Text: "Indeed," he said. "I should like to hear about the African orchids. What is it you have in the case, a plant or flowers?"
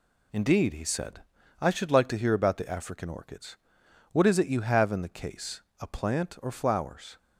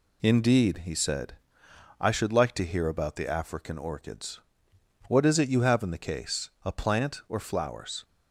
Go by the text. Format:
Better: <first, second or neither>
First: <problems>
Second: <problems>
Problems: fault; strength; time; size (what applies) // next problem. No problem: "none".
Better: neither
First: none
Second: none